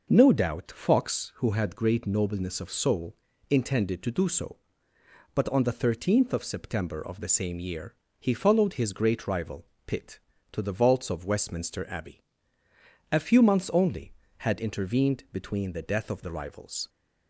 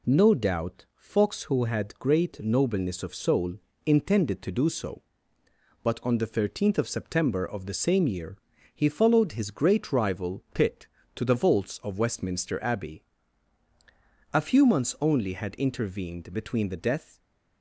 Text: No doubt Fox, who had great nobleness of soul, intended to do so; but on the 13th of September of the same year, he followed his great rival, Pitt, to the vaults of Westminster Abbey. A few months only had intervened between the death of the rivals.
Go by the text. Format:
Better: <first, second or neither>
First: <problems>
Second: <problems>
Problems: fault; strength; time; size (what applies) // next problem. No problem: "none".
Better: first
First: none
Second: stops before "of the rivals"; at 17.1 s